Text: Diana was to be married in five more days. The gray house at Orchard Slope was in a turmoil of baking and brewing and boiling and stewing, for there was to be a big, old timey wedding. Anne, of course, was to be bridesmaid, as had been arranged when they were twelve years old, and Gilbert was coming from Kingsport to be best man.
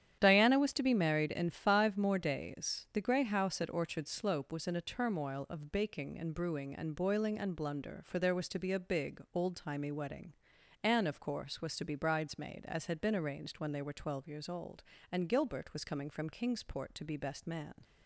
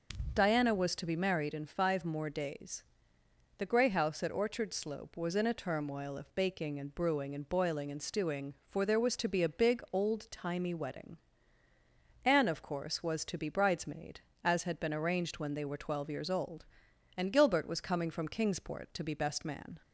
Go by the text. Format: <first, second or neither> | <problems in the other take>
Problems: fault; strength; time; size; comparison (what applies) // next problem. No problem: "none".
second | starts louder than the rest; strong; until 1.2 s; 10 dB; noticeable in the second // says "blunder" for "stewing"; at 7.5 s